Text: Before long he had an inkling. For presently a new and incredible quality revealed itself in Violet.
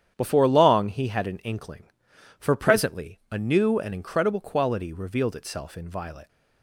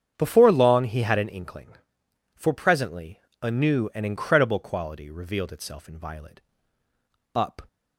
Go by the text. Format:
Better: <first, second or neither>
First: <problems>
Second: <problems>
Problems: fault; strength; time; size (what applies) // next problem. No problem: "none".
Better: first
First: starts louder than the rest; strong; until 1.1 s; 9.5 dB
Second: starts louder than the rest; strong; until 1.1 s; 8 dB // pauses between "presently" and "a"; slight; at 3.1 s; 0.24 s long // goes on to say "Up"; slight; from 7.3 s on; 0.32 s long